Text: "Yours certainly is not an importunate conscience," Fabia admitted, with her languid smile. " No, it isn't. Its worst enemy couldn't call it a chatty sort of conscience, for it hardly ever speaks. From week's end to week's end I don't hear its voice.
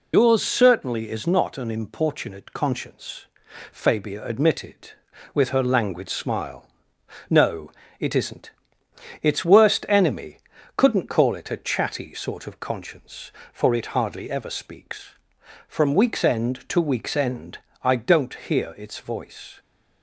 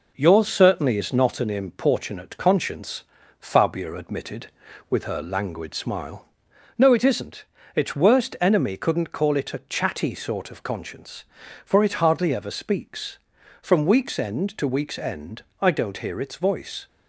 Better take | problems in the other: second | loses the start of "Yours"; at 0.1 s; 75 ms // pauses between "enemy" and "couldn't"; slight; at 10.3 s; 0.36 s long // pauses between "end" and "I"; slight; at 17.5 s; 0.22 s long; slight in the second

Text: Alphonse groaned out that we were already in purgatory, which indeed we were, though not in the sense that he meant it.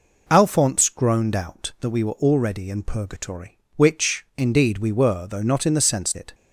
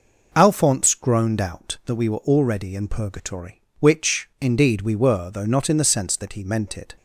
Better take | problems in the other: second | skips "that he meant"; at 6.1 s

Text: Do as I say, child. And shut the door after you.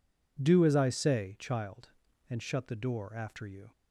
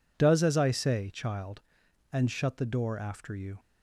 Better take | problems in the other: first | says "Does" for "Do"; at 0.1 s

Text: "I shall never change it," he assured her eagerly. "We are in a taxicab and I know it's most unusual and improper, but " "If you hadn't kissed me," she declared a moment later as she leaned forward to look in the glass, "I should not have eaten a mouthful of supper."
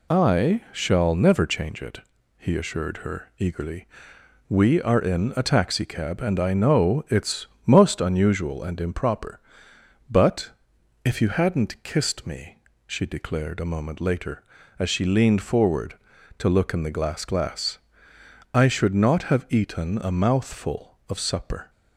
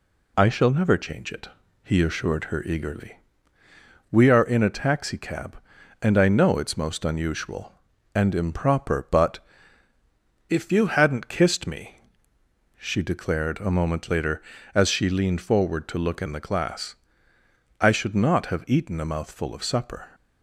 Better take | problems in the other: second | pauses between "it's" and "most"; slight; at 7.4 s; 0.20 s long // says "glass" twice; at 17.2 s

